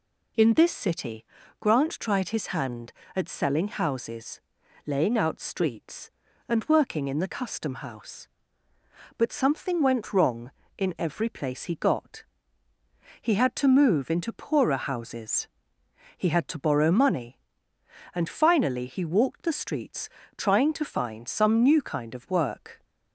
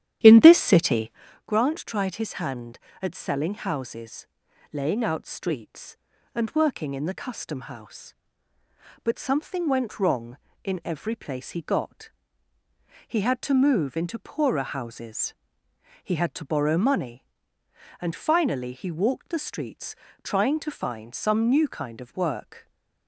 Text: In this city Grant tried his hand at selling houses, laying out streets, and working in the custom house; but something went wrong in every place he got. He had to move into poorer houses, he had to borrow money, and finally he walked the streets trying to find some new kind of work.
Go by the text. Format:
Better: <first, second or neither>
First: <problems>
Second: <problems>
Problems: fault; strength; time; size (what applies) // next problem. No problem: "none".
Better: first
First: pauses between "city" and "Grant"; at 1.2 s; 0.38 s long // pauses between "streets" and "trying"; slight; at 20.0 s; 0.26 s long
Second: starts louder than the rest; strong; until 1.4 s; 11.5 dB // pauses between "city" and "Grant"; at 1.0 s; 0.38 s long // pauses between "streets" and "trying"; slight; at 19.9 s; 0.26 s long